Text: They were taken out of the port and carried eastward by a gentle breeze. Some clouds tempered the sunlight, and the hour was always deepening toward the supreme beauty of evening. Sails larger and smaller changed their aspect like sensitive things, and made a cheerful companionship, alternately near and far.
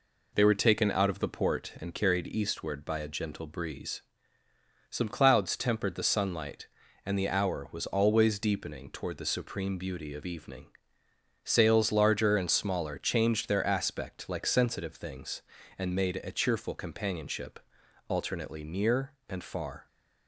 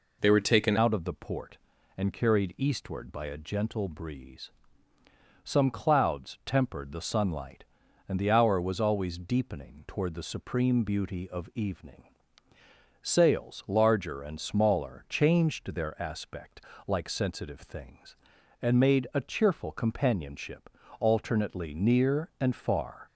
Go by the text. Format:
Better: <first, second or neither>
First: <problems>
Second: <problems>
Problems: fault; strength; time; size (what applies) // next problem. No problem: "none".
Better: first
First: none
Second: changes voice at "out"; from 0.7 s on; 22.3 s long // pauses between "aspect" and "like"; slight; at 16.6 s; 0.26 s long